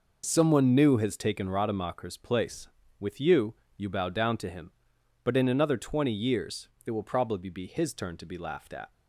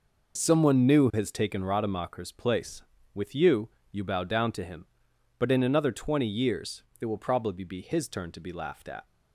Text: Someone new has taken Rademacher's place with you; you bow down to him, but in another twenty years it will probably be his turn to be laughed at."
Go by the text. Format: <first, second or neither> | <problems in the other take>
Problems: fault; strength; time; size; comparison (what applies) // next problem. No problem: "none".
neither | pauses between "years" and "it"; slight; the same in both